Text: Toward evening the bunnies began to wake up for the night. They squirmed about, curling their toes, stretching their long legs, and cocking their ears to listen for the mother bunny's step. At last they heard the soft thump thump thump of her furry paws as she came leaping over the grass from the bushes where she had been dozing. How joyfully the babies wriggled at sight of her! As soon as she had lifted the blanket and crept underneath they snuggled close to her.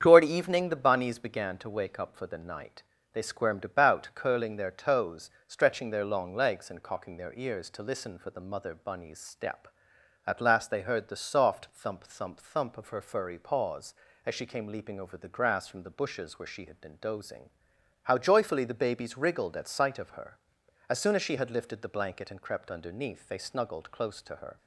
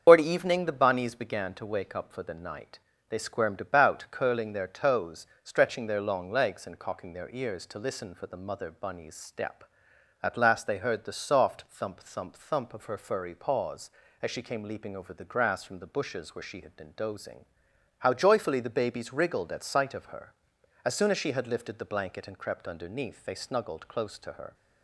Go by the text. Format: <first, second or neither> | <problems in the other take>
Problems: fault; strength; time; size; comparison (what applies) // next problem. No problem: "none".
first | loses the start of "Toward"; at 0.0 s; 105 ms // starts louder than the rest; strong; until 1.0 s; 7 dB; strong in the first